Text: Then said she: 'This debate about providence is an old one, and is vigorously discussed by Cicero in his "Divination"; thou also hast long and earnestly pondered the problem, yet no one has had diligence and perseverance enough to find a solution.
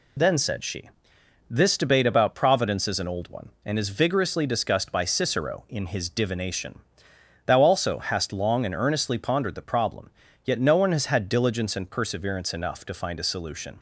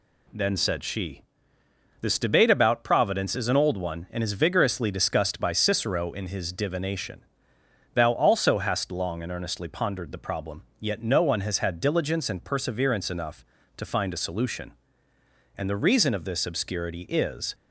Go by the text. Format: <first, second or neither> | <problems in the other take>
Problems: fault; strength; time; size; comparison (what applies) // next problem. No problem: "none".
first | goes on to say "And the reason of this obscurity is"; strong; from 15.5 s on; 1.9 s long